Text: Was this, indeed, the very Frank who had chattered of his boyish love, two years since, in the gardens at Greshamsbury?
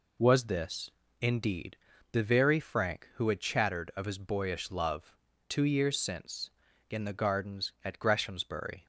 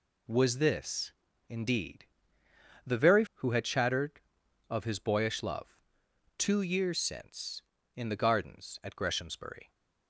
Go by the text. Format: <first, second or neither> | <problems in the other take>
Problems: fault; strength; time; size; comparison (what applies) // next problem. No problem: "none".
first | skips "Frank"; at 3.2 s